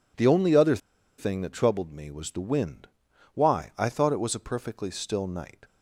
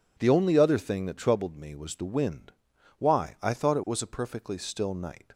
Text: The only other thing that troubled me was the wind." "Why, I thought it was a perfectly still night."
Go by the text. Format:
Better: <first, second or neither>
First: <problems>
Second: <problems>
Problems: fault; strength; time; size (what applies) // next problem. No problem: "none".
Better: second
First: pauses between "other" and "thing"; at 0.7 s; 0.40 s long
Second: none